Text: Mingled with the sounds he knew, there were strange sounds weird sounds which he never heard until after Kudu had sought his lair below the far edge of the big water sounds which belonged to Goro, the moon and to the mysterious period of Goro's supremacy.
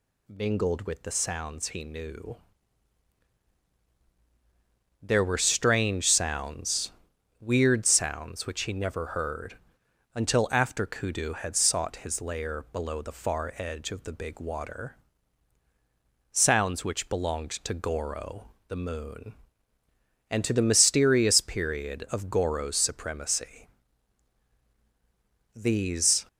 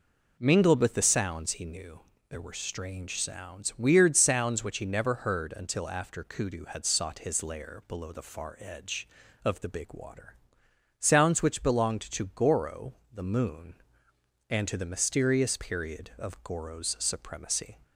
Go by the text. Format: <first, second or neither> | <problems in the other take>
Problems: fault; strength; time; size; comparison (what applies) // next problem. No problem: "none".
second | pauses between "sounds" and "weird"; noticeable; at 6.9 s; 0.48 s long // pauses between "heard" and "until"; noticeable; at 9.5 s; 0.60 s long // pauses between "water" and "sounds"; strong; at 14.9 s; 1.3 s long; noticeable in the second // goes on to say "These"; noticeable; from 25.5 s on; 0.70 s long